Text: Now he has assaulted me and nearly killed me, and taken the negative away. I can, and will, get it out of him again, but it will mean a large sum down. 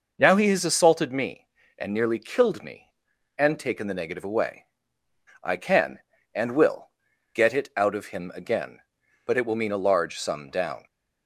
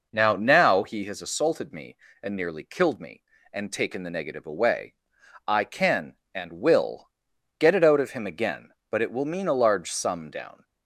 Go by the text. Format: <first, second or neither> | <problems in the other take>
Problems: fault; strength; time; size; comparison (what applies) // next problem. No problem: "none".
first | says "Now" twice; at 0.3 s